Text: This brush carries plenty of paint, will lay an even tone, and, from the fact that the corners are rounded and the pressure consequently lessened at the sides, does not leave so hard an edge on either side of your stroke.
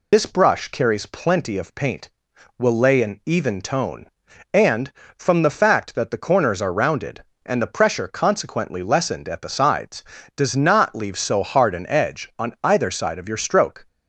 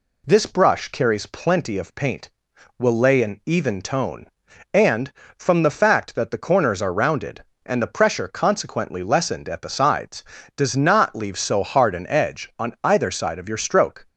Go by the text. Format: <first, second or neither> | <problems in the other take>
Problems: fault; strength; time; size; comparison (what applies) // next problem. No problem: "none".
second | loses the start of "This"; at 0.1 s; 90 ms